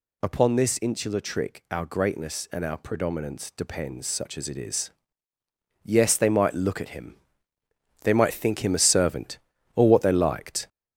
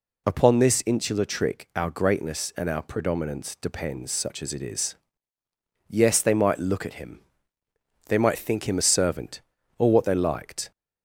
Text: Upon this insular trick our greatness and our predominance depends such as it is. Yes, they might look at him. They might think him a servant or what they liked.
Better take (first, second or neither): second